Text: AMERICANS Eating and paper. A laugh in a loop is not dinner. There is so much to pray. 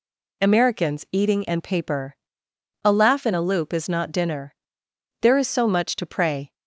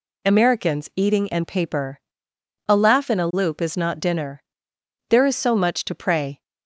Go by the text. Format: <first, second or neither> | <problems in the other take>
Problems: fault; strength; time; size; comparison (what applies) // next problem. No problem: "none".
neither | none